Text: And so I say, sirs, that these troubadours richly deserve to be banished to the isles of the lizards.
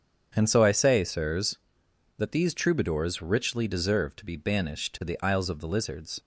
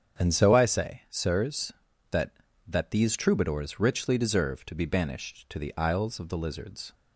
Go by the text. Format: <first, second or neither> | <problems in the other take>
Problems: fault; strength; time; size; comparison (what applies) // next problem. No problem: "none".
first | starts louder than the rest; strong; until 1.2 s; 8 dB; strong in the first // says "that" twice; at 2.6 s